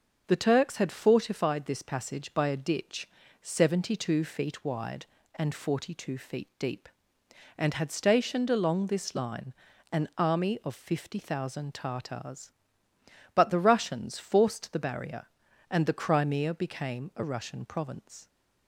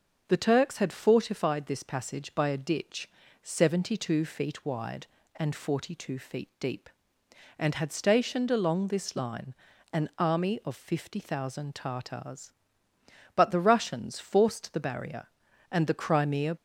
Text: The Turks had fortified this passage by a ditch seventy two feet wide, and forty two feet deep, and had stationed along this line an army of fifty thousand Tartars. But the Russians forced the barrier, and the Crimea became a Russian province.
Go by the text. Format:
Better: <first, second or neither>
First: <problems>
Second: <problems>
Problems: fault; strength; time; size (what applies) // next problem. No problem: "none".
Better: first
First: starts louder than the rest; until 1.2 s; 6.5 dB // pauses between "ditch" and "seventy"; slight; at 3.0 s; 0.36 s long // pauses between "line" and "an"; at 9.5 s; 0.40 s long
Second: starts louder than the rest; until 1.2 s; 6.5 dB // pauses between "ditch" and "seventy"; slight; at 3.0 s; 0.36 s long // pauses between "line" and "an"; at 9.5 s; 0.40 s long // stops before "became a Russian province"; at 16.5 s